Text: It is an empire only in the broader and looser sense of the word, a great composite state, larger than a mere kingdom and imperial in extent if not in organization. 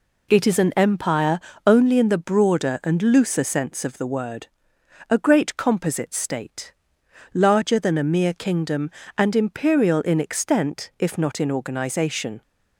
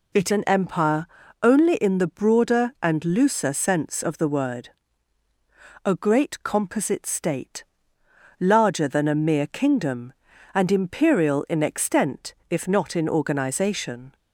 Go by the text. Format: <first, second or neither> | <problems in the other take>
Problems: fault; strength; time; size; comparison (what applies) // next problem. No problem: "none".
first | skips "is"; at 0.3 s // pauses between "empire" and "only"; slight; at 1.0 s; 0.34 s long; slight in the first